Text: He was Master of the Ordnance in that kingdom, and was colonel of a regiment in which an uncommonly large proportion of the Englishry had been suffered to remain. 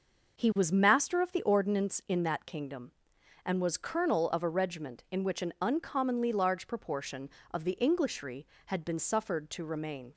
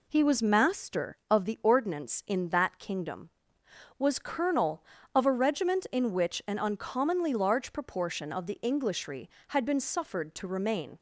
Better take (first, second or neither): first